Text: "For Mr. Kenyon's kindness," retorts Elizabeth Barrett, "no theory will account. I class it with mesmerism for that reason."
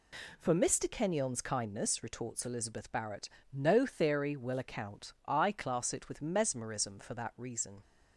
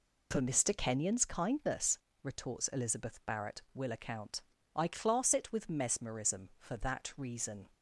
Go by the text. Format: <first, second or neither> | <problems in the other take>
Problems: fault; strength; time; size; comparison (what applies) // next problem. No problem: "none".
first | skips "no theory"; at 3.6 s